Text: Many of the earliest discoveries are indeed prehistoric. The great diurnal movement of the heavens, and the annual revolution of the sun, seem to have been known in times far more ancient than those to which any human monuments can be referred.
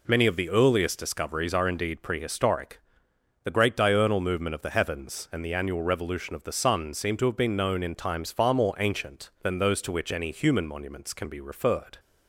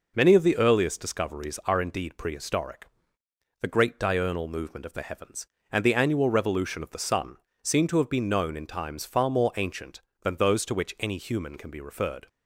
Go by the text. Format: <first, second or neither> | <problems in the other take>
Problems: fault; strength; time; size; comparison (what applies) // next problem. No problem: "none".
first | skips "monuments"; at 11.5 s